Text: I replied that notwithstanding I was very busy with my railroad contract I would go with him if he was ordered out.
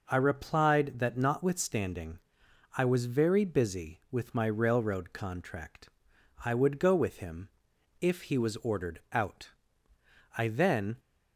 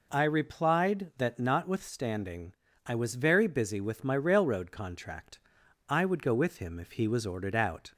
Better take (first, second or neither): second